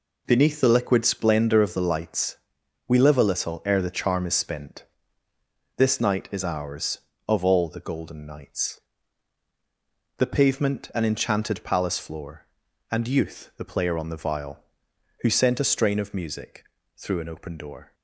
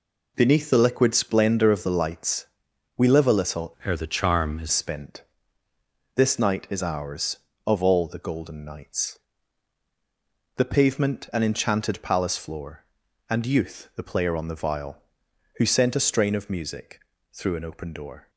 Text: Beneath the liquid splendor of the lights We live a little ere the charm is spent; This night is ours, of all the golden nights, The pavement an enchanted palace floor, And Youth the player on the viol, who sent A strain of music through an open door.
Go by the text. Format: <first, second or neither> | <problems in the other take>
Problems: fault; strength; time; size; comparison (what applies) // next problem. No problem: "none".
first | pauses between "lights" and "We"; noticeable; at 2.4 s; 0.50 s long; noticeable in the first // changes voice from "ere" to "is"; from 3.8 to 4.6 s; 0.8 s long // pauses between "music" and "through"; slight; at 16.9 s; 0.30 s long; slight in the first